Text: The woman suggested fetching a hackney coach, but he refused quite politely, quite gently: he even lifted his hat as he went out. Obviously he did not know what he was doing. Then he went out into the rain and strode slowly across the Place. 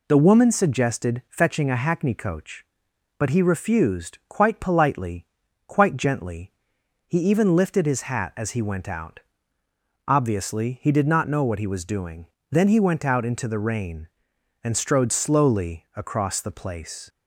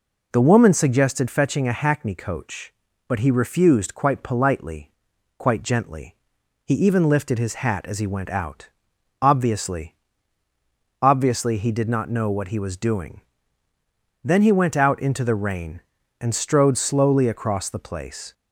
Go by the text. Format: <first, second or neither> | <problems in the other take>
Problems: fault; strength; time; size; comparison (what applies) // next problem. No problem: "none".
first | says "Obviously" twice; at 11.0 s